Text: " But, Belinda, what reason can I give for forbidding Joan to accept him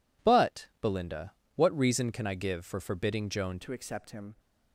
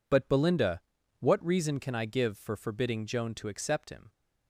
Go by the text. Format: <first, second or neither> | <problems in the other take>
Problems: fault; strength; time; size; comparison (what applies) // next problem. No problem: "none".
second | changes voice at "to"; from 3.6 s on; 0.7 s long